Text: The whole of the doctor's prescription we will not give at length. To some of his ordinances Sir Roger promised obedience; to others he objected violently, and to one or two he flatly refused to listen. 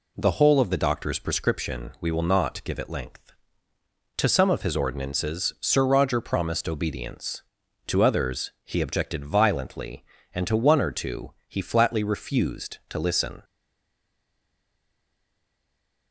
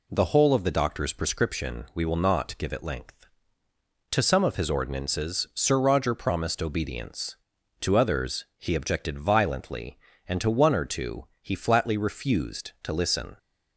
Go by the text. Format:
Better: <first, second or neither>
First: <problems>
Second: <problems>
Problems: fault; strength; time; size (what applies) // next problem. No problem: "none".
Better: second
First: pauses between "two" and "he"; slight; at 11.3 s; 0.16 s long // stays silent after the last word; strong; from 13.4 s on; 2.7 s long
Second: pauses between "two" and "he"; slight; at 11.2 s; 0.16 s long